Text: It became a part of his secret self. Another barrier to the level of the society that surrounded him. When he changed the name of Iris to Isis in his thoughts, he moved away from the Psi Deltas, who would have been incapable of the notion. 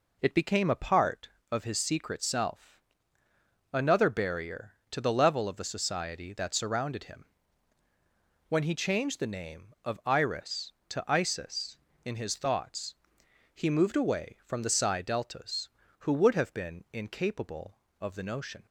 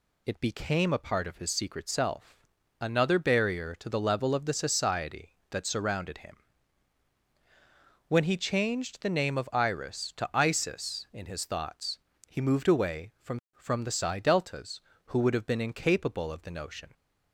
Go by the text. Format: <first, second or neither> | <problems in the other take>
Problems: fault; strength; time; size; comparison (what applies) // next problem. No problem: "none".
first | says "from" twice; at 13.5 s